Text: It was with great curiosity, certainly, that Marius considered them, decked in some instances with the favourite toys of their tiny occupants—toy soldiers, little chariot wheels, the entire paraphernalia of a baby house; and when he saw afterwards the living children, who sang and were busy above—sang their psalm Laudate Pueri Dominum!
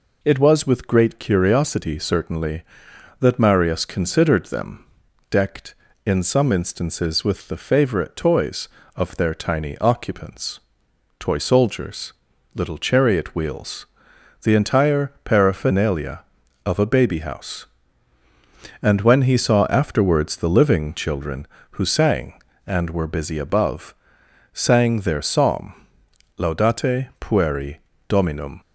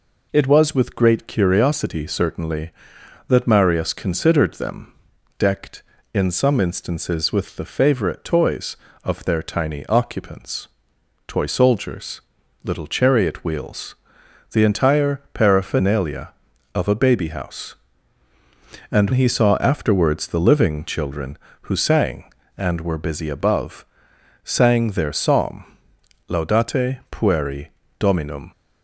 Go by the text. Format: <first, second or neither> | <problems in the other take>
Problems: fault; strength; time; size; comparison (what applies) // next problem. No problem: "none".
first | skips "when"; at 19.1 s // pauses between "psalm" and "Laudate"; noticeable; at 25.6 s; 0.64 s long; noticeable in the first // pauses between "Pueri" and "Dominum"; slight; at 27.6 s; 0.30 s long; slight in the first